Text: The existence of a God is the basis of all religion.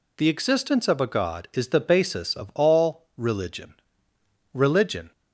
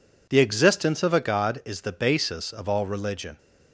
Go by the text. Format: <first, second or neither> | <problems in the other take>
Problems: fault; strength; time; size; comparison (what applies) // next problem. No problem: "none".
second | says "religion" twice; at 4.5 s